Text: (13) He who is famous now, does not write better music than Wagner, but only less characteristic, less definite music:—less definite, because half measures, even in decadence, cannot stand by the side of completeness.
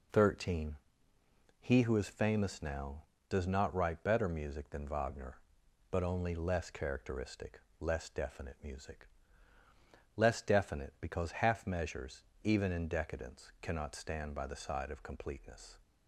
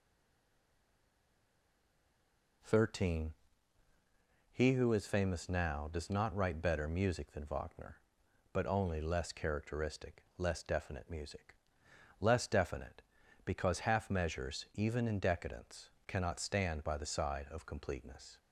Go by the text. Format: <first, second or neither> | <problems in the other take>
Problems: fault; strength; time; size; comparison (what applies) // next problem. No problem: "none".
first | stays silent before the first word; strong; until 2.6 s; 2.6 s long